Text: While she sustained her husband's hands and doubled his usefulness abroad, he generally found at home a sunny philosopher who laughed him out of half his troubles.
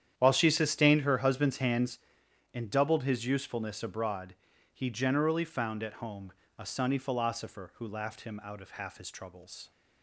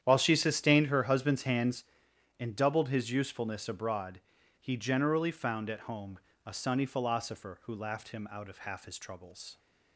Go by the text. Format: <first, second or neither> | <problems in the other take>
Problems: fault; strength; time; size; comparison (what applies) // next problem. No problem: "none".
neither | starts louder than the rest; strong; the same in both // pauses between "home" and "a"; slight; the same in both